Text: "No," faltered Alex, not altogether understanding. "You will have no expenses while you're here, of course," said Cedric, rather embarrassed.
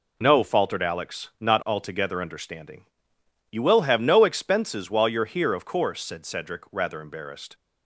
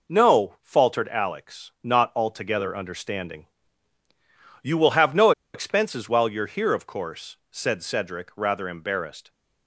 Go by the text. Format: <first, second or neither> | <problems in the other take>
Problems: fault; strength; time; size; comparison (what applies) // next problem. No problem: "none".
first | pauses between "no" and "expenses"; slight; at 5.3 s; 0.23 s long